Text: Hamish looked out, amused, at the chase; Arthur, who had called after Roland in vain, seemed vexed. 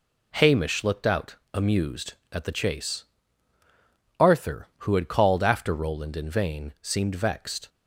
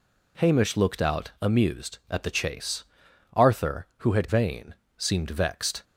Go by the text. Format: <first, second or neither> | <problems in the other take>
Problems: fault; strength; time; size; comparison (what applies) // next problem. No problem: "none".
first | skips "called after Roland in"; at 4.2 s